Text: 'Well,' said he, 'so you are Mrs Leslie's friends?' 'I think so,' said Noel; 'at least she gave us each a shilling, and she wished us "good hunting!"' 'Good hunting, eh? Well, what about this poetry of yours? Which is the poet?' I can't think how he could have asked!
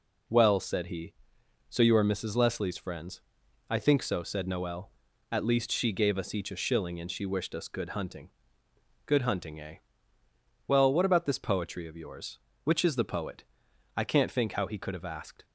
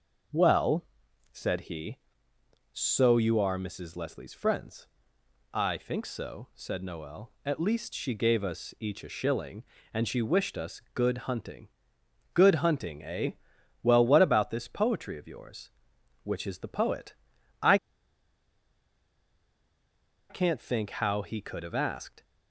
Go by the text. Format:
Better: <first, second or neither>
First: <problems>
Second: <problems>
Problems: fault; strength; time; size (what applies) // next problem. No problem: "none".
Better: first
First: none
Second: starts louder than the rest; noticeable; until 1.7 s; 6 dB // pauses between "I" and "can't"; strong; at 17.7 s; 2.5 s long